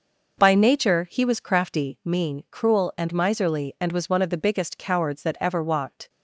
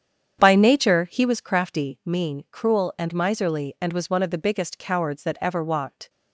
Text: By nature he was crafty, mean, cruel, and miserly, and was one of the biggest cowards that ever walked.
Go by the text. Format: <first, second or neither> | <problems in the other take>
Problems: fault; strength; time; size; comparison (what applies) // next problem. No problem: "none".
first | starts louder than the rest; strong; until 1.3 s; 8.5 dB